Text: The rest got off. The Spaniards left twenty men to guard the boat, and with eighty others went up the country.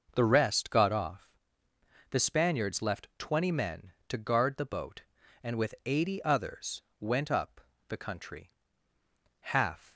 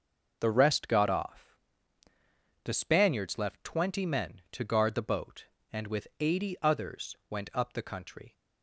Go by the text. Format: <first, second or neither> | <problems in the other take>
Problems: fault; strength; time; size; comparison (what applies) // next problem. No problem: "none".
second | pauses between "others" and "went"; slight; at 6.8 s; 0.18 s long // pauses between "up" and "the"; slight; at 7.5 s; 0.30 s long // goes on to say "Half"; from 9.3 s on; 0.54 s long